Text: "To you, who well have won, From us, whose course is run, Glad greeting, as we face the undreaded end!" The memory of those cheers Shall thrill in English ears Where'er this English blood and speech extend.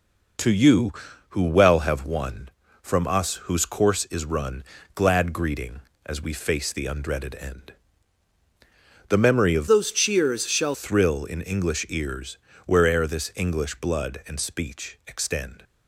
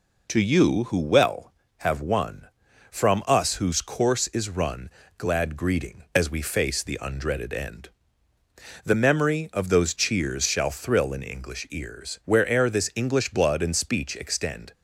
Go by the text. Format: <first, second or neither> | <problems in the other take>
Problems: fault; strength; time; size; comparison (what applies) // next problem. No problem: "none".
second | changes voice from "those" to "Shall"; from 9.6 to 10.7 s; 1.1 s long // pauses between "ears" and "Where'er"; slight; at 12.3 s; 0.28 s long